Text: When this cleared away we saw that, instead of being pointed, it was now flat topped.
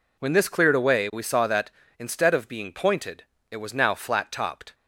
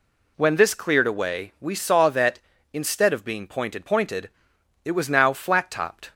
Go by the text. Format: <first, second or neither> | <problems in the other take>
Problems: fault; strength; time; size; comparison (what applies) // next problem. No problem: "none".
first | says "pointed" twice; at 3.8 s